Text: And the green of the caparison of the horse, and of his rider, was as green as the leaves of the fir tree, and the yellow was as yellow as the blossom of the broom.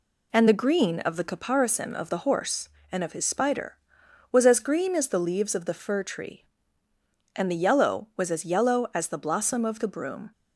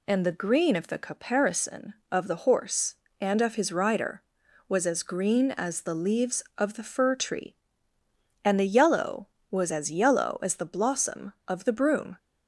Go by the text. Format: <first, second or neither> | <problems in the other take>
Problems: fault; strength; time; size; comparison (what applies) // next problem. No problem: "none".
second | says "spider" for "rider"; at 3.2 s